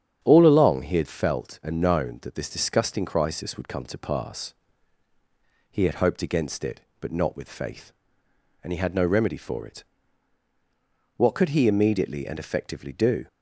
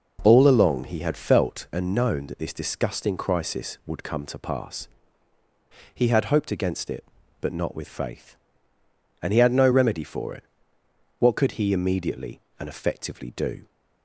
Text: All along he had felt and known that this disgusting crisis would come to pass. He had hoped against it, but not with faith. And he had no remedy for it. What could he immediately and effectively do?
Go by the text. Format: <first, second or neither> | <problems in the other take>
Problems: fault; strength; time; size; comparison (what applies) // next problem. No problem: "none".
second | starts louder than the rest; strong; until 1.4 s; 8.5 dB